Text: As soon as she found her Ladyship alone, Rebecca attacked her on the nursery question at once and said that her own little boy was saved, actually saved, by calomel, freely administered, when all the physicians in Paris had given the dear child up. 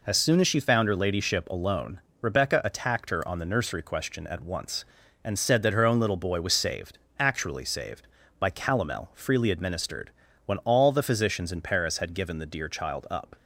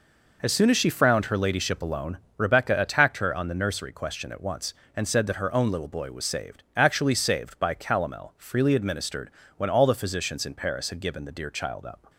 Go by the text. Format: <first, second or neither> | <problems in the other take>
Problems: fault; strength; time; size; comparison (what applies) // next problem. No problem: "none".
first | says "frowned" for "found"; at 0.8 s